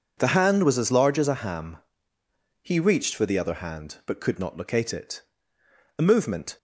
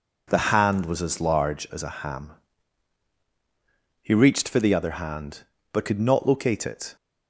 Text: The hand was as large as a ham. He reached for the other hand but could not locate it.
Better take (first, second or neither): second